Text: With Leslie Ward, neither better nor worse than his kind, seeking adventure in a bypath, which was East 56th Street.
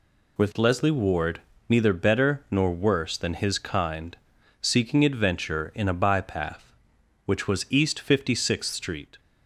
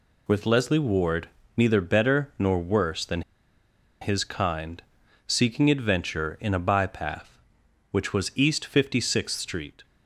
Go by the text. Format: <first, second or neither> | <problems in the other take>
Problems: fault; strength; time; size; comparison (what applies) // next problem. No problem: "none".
first | pauses between "than" and "his"; noticeable; at 3.2 s; 0.80 s long